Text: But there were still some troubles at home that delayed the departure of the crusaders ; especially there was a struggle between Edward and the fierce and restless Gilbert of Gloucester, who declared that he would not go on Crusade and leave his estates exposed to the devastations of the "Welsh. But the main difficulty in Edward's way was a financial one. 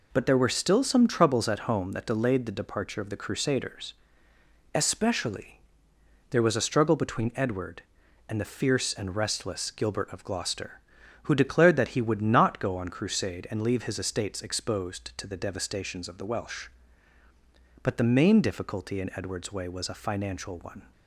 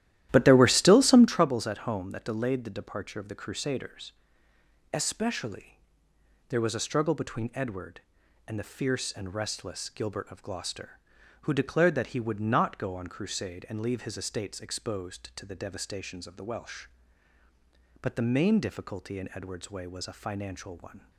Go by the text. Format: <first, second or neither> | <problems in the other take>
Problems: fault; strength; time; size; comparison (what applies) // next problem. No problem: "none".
first | starts louder than the rest; strong; until 1.5 s; 13 dB // pauses between "especially" and "there"; noticeable; at 5.8 s; 0.70 s long; noticeable in the first